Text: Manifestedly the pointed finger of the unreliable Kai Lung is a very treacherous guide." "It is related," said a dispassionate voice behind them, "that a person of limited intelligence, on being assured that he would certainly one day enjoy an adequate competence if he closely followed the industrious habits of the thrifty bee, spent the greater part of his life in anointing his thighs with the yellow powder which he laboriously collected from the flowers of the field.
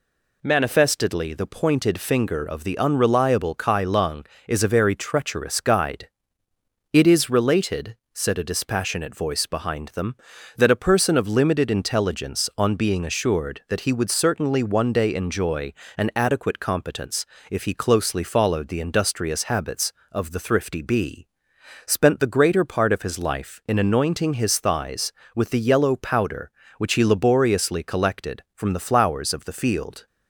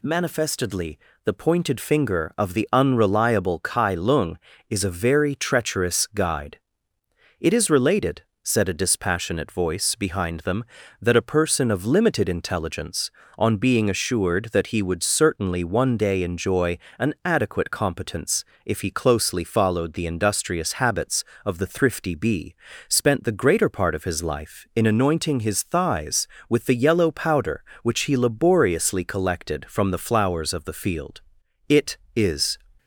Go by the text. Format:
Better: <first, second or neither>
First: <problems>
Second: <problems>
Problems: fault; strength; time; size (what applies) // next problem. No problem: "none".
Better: first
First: pauses between "enjoy" and "an"; slight; at 15.7 s; 0.24 s long // pauses between "competence" and "if"; slight; at 17.2 s; 0.24 s long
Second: pauses between "Manifestedly" and "the"; slight; at 0.9 s; 0.28 s long // pauses between "enjoy" and "an"; slight; at 16.7 s; 0.22 s long // pauses between "competence" and "if"; slight; at 18.4 s; 0.22 s long // goes on to say "It is"; noticeable; from 31.6 s on; 0.90 s long